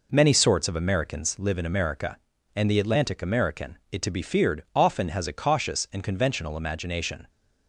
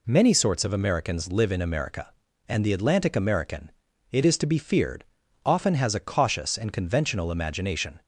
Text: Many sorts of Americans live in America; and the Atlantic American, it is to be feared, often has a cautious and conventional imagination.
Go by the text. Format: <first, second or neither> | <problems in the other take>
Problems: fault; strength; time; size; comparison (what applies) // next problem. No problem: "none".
second | skips "is"; at 4.0 s